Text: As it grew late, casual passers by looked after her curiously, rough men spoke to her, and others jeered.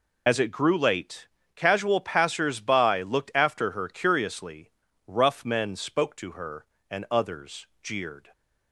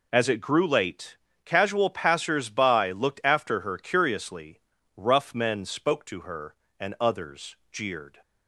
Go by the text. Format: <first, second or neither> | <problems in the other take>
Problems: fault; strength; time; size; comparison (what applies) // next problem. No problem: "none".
second | loses the start of "As"; at 0.2 s; 45 ms // pauses between "others" and "jeered"; slight; at 7.6 s; 0.16 s long; slight in the second